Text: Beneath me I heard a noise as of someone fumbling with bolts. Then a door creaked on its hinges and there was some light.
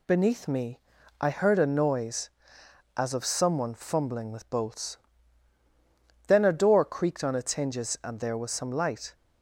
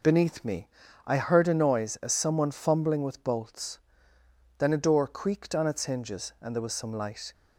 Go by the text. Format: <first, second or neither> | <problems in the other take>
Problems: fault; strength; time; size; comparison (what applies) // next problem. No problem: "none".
first | pauses between "me" and "I"; at 0.6 s; 0.40 s long; also in the first // skips "of"; at 2.1 s